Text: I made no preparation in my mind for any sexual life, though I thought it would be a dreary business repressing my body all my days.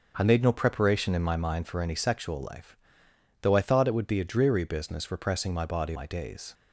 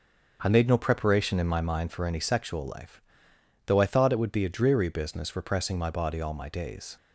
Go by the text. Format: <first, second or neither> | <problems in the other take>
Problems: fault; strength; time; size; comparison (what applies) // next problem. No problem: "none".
second | starts louder than the rest; until 1.1 s; 6 dB; also in the second // skips "all"; at 5.9 s